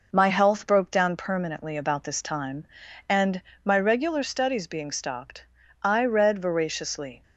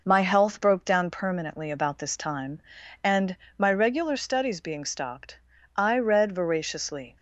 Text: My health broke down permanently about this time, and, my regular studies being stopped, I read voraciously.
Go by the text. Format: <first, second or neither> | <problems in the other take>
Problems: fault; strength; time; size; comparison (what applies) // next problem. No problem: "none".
neither | none